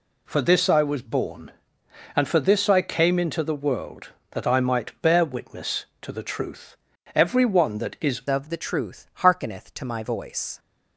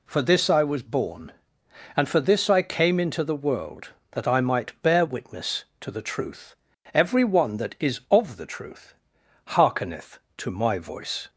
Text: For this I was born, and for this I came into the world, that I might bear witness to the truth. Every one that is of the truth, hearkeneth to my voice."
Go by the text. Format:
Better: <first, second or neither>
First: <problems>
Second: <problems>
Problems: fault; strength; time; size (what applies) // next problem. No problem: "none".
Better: second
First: changes voice at "of"; from 8.2 s on; 2.3 s long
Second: none